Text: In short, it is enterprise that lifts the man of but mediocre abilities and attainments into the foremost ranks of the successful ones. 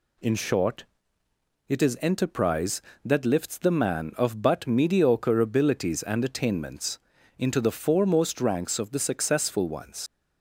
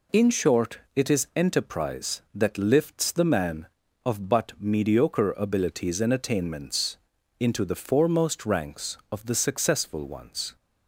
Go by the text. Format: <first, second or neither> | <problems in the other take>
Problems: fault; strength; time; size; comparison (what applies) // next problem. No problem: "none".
second | pauses between "attainments" and "into"; at 6.9 s; 0.40 s long; also in the second // leaves "ones" unfinished; at 10.0 s; 95 ms